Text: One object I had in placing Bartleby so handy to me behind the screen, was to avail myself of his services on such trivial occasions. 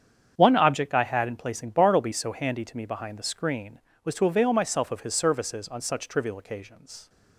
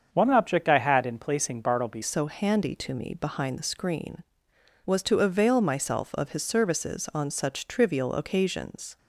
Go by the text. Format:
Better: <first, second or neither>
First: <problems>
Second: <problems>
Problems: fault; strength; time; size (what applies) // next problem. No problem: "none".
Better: first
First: starts louder than the rest; strong; until 1.3 s; 8 dB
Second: starts louder than the rest; strong; until 1.1 s; 7 dB // changes voice at "so"; from 2.0 s on; 6.9 s long